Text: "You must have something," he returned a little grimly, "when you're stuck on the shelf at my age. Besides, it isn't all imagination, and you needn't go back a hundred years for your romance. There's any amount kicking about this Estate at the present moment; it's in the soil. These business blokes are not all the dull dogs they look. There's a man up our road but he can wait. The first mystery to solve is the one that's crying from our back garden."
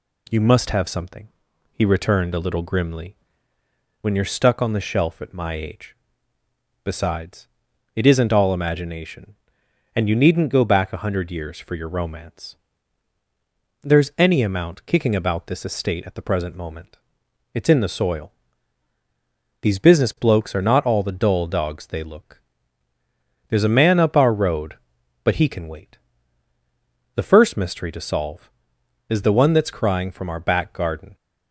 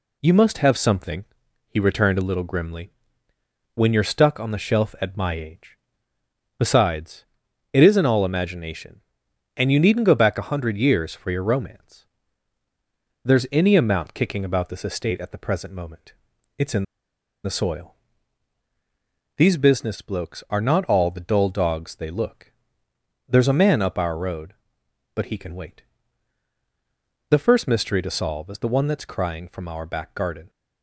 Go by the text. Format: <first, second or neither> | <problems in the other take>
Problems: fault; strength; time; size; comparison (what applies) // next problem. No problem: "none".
first | pauses between "in" and "the"; noticeable; at 16.8 s; 0.59 s long